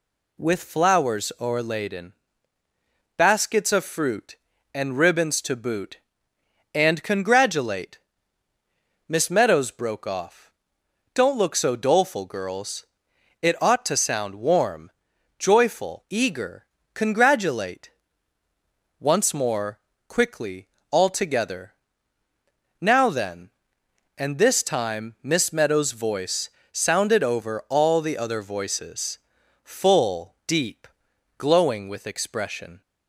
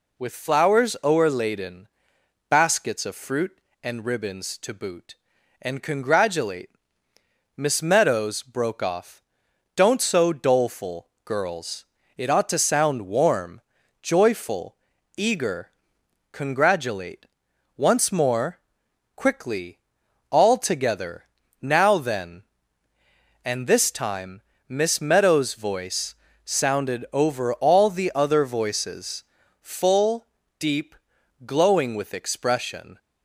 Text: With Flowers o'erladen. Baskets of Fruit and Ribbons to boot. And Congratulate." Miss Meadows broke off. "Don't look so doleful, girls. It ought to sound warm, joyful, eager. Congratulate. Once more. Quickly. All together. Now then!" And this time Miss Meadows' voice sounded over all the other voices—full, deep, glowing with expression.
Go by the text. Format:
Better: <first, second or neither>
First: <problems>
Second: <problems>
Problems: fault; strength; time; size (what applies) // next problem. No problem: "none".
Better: first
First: pauses between "voice" and "sounded"; slight; at 26.4 s; 0.22 s long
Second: skips "look"; at 10.0 s // pauses between "time" and "Miss"; slight; at 24.4 s; 0.26 s long // pauses between "voice" and "sounded"; slight; at 26.1 s; 0.30 s long